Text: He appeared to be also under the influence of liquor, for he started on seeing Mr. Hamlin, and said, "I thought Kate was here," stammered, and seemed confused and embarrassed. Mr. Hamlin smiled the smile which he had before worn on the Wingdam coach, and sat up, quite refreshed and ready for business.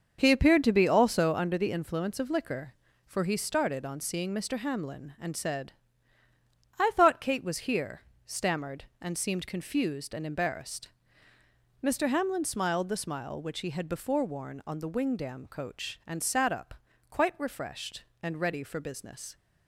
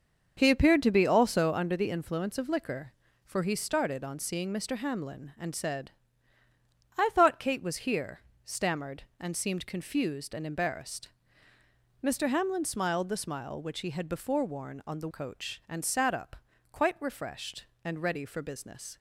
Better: first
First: starts louder than the rest; until 1.2 s; 6.5 dB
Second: starts louder than the rest; until 1.3 s; 6.5 dB // skips "Wingdam"; at 15.0 s

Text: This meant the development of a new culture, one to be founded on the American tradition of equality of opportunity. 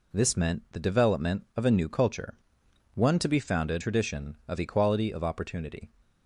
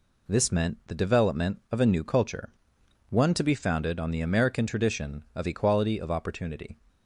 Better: second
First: skips "on the American"; at 3.8 s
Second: none

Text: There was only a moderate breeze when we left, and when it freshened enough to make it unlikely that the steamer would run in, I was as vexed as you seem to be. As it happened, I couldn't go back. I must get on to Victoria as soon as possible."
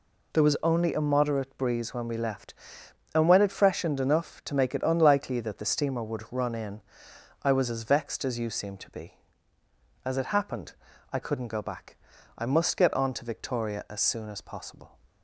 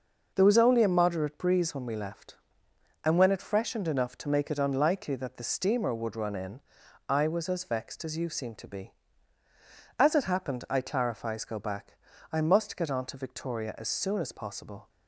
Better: first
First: none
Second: says "clarifies" for "couldn't"; at 10.8 s

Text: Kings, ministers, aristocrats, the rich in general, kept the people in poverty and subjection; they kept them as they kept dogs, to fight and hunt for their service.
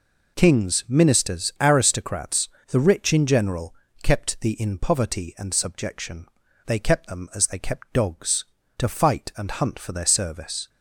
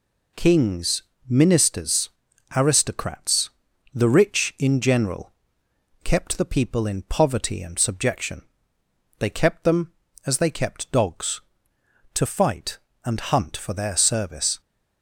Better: second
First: skips "people"; at 4.5 s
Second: none

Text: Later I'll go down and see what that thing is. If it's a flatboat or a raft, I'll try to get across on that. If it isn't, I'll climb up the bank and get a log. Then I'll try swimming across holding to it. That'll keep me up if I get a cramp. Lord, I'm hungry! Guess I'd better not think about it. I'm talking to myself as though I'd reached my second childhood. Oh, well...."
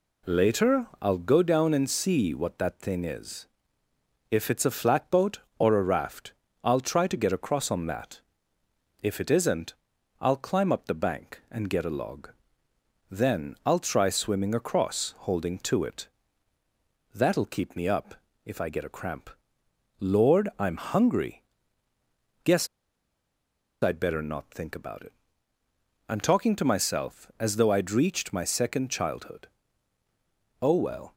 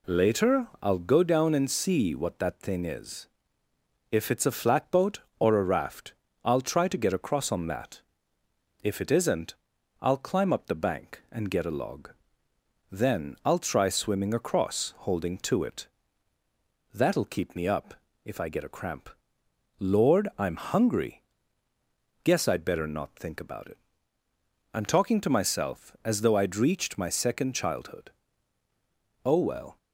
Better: second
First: pauses between "Later" and "I'll"; slight; at 0.8 s; 0.16 s long // pauses between "up" and "if"; slight; at 18.1 s; 0.30 s long // pauses between "Guess" and "I'd"; at 22.6 s; 1.1 s long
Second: pauses between "Later" and "I'll"; slight; at 0.6 s; 0.16 s long // pauses between "up" and "if"; slight; at 17.9 s; 0.30 s long

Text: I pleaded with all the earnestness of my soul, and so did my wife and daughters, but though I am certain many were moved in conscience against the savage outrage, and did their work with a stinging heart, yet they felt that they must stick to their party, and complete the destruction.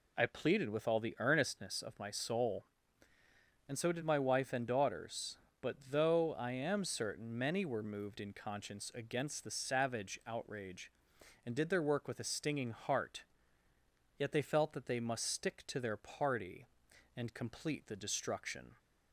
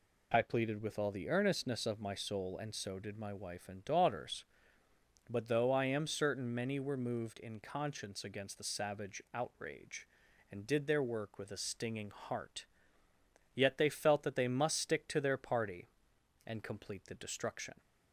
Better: neither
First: none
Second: none

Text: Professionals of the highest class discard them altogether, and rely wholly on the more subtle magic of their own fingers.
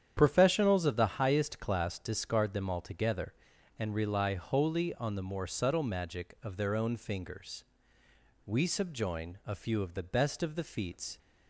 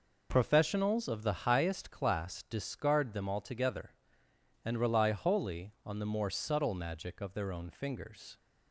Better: second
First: starts louder than the rest; strong; until 1.1 s; 9 dB // goes on to say "We subjoin a few of the best of the feats"; strong; from 8.4 s on; 2.7 s long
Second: none

